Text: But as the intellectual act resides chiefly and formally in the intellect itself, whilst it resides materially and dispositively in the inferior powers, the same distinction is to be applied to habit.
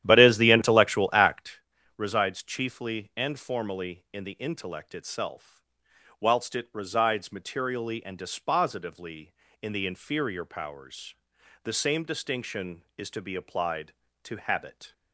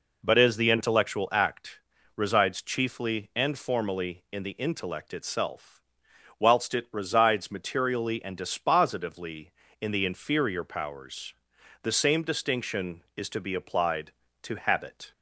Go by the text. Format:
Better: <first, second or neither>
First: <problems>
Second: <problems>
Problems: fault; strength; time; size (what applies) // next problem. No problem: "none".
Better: second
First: starts louder than the rest; strong; until 1.6 s; 11.5 dB // pauses between "act" and "resides"; slight; at 1.6 s; 0.36 s long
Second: pauses between "act" and "resides"; slight; at 1.7 s; 0.36 s long